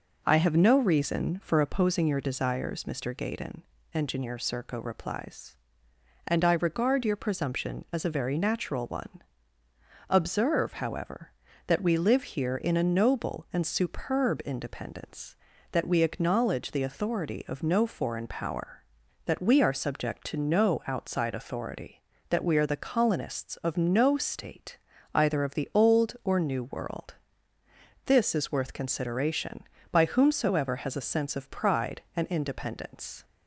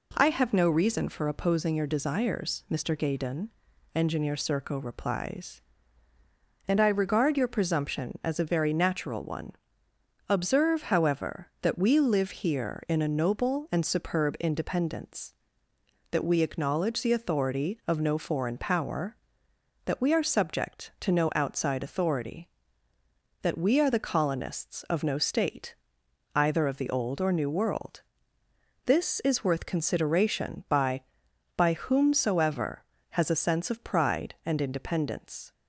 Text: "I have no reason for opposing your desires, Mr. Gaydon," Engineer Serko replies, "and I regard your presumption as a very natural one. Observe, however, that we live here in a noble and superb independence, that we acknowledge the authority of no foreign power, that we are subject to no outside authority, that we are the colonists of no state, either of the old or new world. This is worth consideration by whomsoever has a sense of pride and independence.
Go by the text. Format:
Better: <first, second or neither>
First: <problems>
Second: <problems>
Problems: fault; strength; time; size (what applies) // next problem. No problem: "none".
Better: first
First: none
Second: says "by" twice; at 31.5 s